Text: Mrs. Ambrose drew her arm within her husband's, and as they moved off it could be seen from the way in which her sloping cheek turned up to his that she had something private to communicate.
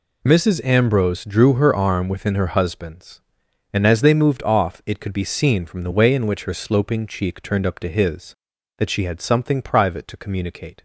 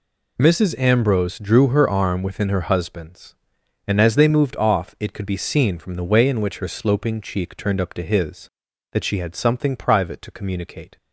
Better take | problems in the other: neither | none

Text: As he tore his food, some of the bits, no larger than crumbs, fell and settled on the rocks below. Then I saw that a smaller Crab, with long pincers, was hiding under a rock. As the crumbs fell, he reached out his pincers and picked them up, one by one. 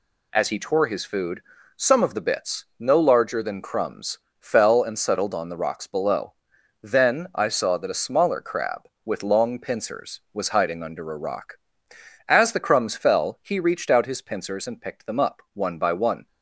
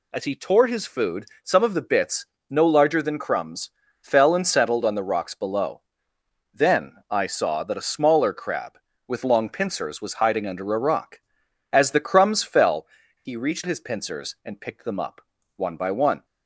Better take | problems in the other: first | skips "out"; at 13.6 s

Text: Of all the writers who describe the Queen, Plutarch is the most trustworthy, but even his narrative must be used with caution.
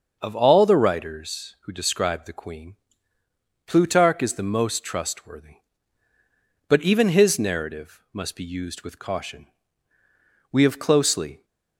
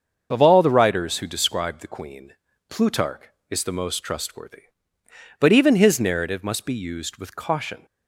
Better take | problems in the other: second | starts louder than the rest; until 1.2 s; 6.5 dB; also in the second // goes on to say "We have closely"; noticeable; from 10.5 s on; 0.94 s long

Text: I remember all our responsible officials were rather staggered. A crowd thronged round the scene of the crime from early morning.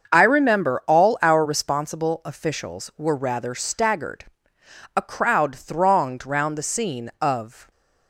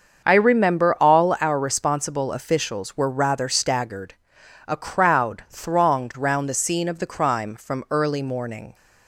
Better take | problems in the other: second | starts louder than the rest; until 1.1 s; 6.5 dB; also in the second // stops before "the crime from early morning"; at 7.7 s

